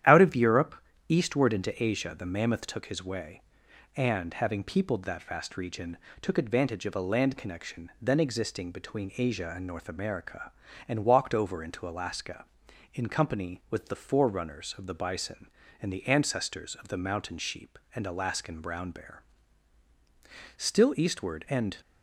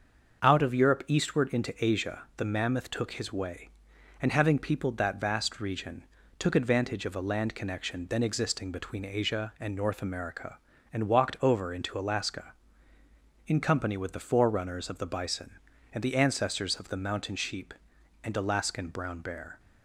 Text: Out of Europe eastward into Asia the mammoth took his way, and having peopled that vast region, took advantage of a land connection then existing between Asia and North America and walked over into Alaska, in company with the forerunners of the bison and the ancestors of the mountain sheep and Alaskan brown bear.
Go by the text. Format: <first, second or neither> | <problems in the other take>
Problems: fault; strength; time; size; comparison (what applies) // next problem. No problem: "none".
second | starts louder than the rest; strong; until 1.4 s; 11 dB; also in the second // pauses between "Europe" and "eastward"; slight; at 0.7 s; 0.34 s long // goes on to say "Still eastward and"; noticeable; from 20.5 s on; 1.2 s long